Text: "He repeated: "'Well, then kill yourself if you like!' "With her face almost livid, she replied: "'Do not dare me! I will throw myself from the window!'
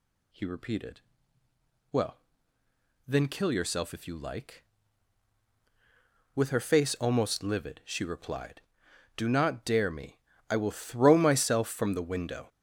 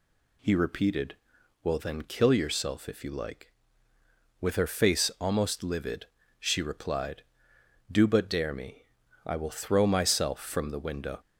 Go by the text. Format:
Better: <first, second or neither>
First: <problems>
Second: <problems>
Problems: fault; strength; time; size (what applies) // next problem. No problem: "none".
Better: first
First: none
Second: says "but" for "not"; at 8.0 s